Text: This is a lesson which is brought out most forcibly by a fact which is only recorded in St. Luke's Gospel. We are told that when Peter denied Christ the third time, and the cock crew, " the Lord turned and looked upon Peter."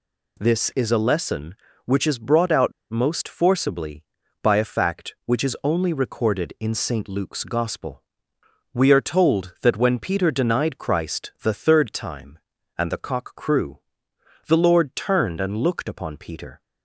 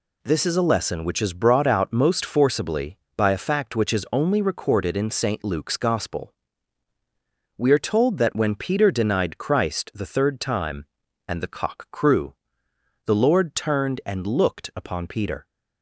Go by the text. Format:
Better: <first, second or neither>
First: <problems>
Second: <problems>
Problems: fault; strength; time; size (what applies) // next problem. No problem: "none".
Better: second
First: pauses between "out" and "most"; slight; at 2.7 s; 0.18 s long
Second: none